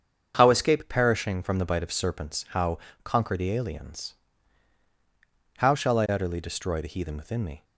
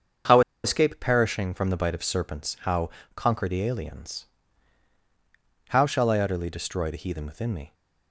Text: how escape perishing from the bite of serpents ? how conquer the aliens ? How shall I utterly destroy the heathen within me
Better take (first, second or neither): first